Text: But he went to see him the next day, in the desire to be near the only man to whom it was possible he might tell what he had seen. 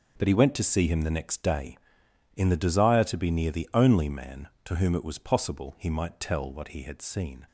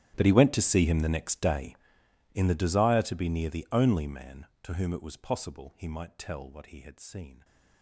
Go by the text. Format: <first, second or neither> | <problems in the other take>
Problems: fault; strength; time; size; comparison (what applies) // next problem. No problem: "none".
first | gets quieter; strong; throughout; 22 dB